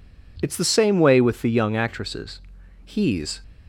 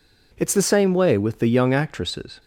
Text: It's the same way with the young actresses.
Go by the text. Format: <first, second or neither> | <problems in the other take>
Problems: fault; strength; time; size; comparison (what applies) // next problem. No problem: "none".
second | goes on to say "He's"; from 2.8 s on; 0.58 s long